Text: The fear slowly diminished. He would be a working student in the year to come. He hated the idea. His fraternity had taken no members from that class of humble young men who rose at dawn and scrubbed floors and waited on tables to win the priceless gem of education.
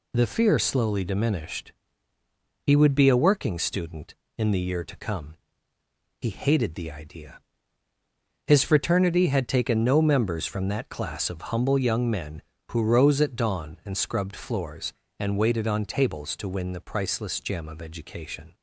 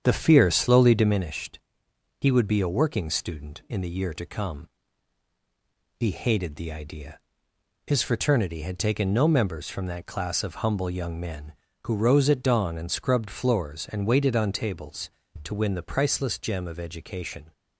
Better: first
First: none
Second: starts louder than the rest; strong; until 1.2 s; 8 dB

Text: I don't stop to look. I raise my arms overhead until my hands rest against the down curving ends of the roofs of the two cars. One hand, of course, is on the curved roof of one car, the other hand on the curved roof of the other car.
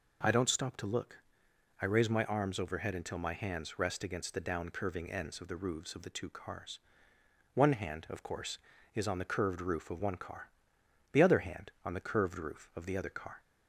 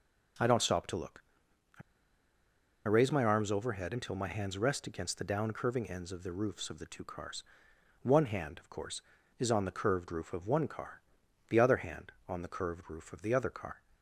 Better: first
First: none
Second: pauses between "I" and "raise"; at 1.8 s; 1.0 s long

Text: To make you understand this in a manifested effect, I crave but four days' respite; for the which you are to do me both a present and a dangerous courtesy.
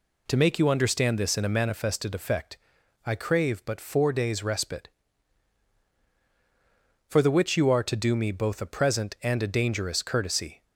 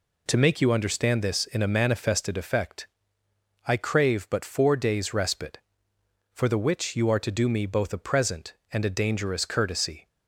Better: neither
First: none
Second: none

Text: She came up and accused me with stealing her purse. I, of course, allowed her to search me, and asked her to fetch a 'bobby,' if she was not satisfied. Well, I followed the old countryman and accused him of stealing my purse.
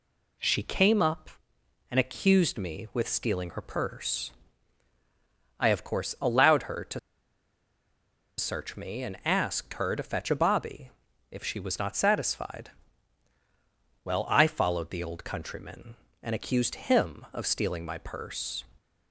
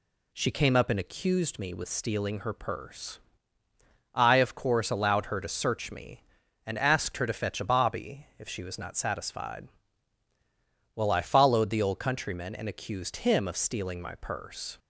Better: second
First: pauses between "to" and "search"; strong; at 6.9 s; 1.4 s long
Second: none

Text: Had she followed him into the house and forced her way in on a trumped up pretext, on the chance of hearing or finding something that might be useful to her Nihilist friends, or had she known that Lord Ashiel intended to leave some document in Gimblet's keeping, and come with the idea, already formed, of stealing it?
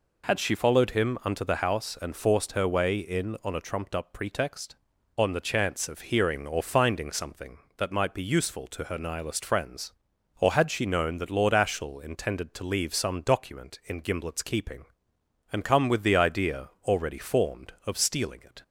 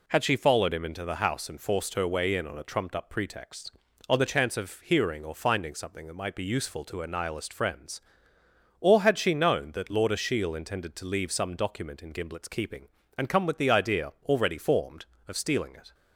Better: second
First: says "unto" for "into"; at 1.2 s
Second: none

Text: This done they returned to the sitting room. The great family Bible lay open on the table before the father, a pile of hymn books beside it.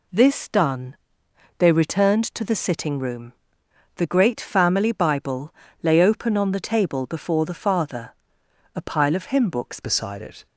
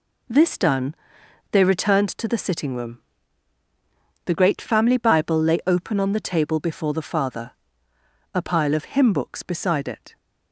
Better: second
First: pauses between "done" and "they"; noticeable; at 0.9 s; 0.64 s long // pauses between "Bible" and "lay"; slight; at 5.5 s; 0.30 s long // changes voice at "beside"; from 9.8 s on; 0.6 s long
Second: pauses between "done" and "they"; noticeable; at 0.9 s; 0.58 s long

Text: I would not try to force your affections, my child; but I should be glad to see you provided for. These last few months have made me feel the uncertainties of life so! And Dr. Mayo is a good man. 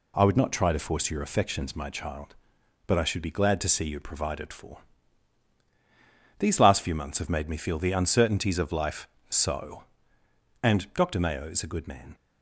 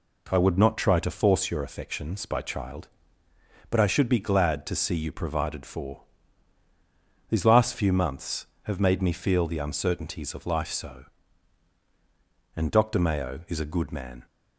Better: first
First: none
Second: says "by" for "my"; at 2.2 s

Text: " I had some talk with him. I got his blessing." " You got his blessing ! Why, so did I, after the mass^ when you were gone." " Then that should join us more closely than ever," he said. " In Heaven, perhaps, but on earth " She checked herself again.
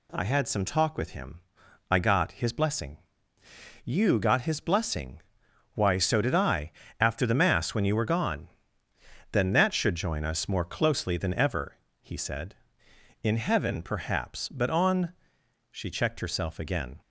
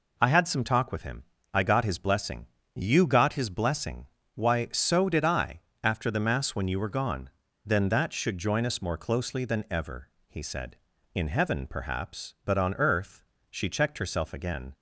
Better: second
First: skips "earth"; at 15.2 s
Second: none

